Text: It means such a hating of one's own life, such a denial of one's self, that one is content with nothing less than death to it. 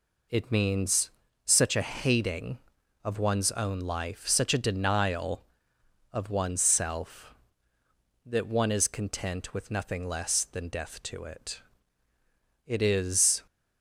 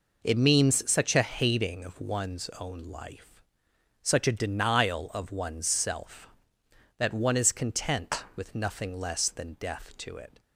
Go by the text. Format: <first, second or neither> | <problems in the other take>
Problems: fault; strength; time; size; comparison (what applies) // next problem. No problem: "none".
second | pauses between "means" and "such"; slight; at 1.0 s; 0.34 s long // goes on to say "It is"; noticeable; from 12.6 s on; 0.80 s long